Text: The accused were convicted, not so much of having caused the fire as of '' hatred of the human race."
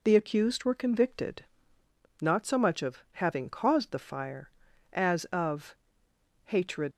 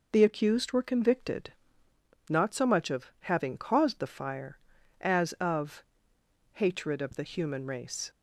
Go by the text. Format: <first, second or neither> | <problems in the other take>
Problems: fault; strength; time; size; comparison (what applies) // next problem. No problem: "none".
second | stops before "of the human race"; at 6.9 s